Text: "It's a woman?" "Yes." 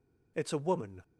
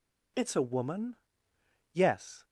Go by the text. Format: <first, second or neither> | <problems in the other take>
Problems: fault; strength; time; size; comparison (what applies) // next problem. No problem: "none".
second | stops before "Yes"; at 1.0 s